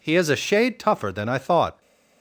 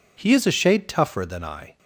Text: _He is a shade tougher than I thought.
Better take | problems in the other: first | stops before "thought"; at 1.7 s

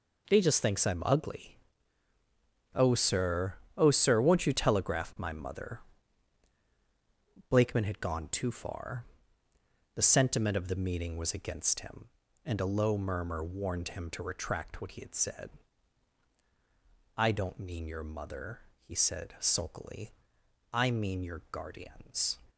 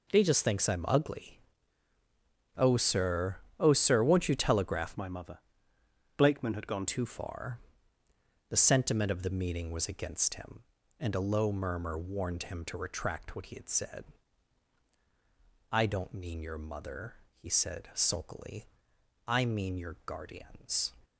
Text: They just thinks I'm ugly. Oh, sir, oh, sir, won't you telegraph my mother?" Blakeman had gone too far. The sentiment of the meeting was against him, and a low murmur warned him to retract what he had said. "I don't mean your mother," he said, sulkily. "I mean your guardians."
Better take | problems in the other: first | changes voice from "my" to "gone"; from 4.9 to 6.8 s; 1.9 s long

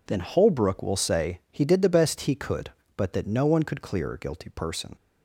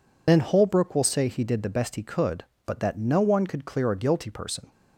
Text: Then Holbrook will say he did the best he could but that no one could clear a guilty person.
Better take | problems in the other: first | loses the start of "Then"; at 0.2 s; 60 ms

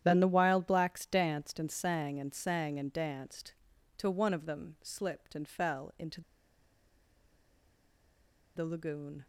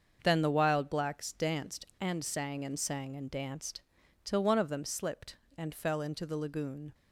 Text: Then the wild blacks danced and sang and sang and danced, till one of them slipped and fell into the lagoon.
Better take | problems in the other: second | starts louder than the rest; strong; until 1.0 s; 10.5 dB; also in the second // pauses between "into" and "the"; strong; at 6.2 s; 2.3 s long

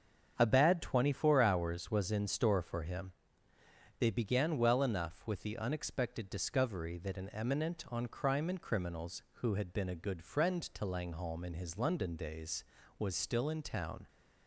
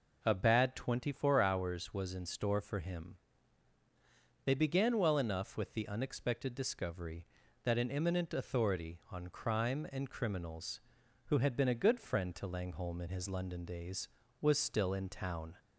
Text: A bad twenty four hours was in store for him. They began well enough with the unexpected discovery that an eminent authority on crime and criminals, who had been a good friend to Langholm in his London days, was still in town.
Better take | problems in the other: second | starts louder than the rest; until 1.3 s; 7 dB // skips "authority"; at 7.8 s

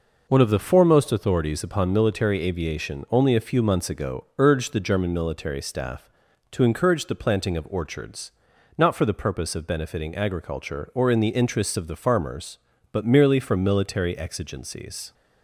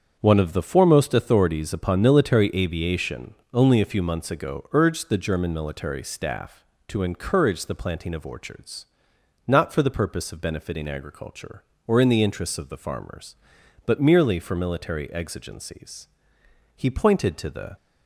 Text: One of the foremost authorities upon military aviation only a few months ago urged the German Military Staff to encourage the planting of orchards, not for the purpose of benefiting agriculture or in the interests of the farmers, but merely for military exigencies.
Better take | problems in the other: first | starts louder than the rest; strong; until 1.2 s; 7.5 dB // pauses between "aviation" and "only"; slight; at 3.3 s; 0.18 s long // goes on to say "He pointed to the"; noticeable; from 16.7 s on; 1.0 s long

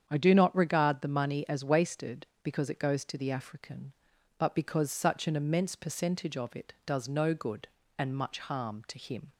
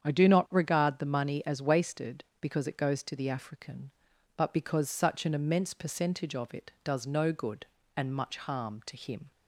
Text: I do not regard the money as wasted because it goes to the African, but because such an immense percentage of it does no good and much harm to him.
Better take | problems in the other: neither | starts louder than the rest; strong; the same in both

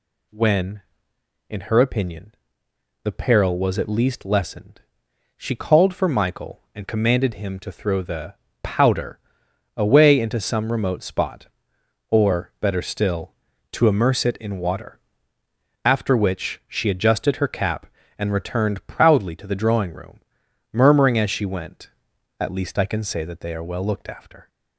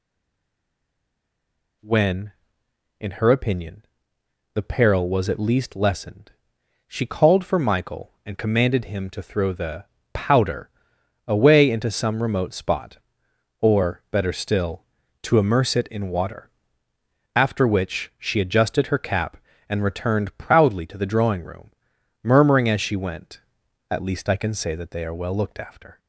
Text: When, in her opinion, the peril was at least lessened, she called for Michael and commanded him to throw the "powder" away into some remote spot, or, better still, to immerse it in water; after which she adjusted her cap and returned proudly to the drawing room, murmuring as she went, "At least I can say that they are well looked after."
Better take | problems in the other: first | stays silent before the first word; noticeable; until 1.8 s; 1.8 s long // pauses between "the" and "powder"; slight; at 9.8 s; 0.26 s long; slight in the first // pauses between "powder" and "away"; noticeable; at 10.6 s; 0.56 s long; noticeable in the first

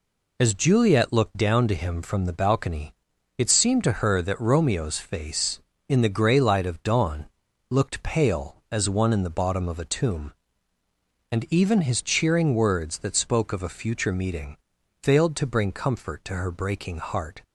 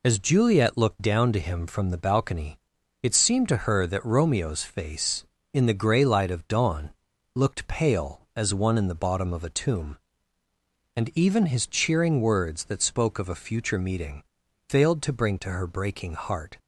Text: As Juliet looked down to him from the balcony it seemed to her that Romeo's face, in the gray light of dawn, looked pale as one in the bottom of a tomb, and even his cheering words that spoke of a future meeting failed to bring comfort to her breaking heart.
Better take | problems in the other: first | pauses between "balcony" and "it"; at 2.5 s; 0.44 s long; also in the first // pauses between "meeting" and "failed"; at 14.2 s; 0.44 s long; also in the first // skips "comfort"; at 15.3 s

